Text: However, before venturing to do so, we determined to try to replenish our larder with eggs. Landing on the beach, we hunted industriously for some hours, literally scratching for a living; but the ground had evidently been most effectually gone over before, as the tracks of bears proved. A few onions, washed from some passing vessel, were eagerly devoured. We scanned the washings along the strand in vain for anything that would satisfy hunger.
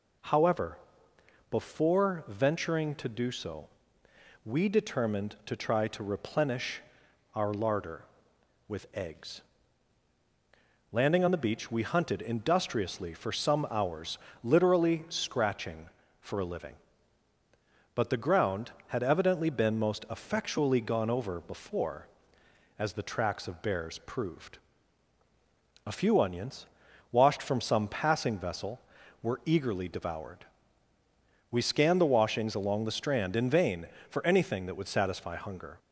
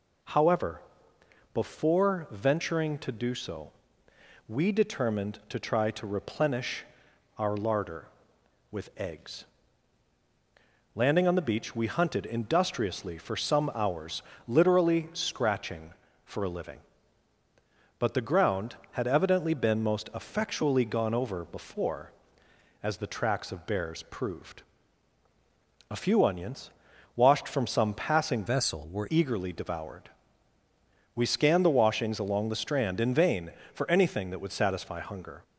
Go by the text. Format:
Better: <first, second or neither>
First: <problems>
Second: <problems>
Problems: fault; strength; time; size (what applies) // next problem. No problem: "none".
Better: first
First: pauses between "replenish" and "our"; noticeable; at 6.8 s; 0.54 s long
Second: pauses between "replenish" and "our"; noticeable; at 6.8 s; 0.54 s long // changes voice from "vessel" to "were"; from 28.4 to 29.0 s; 0.6 s long